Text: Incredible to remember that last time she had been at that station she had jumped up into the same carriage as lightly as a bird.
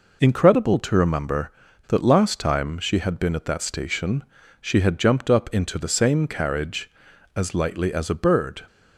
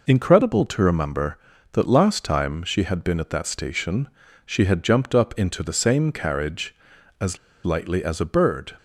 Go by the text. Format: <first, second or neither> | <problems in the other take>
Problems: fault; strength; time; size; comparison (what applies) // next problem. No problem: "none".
first | pauses between "station" and "she"; at 4.0 s; 0.38 s long; also in the first // pauses between "as" and "lightly"; slight; at 7.3 s; 0.26 s long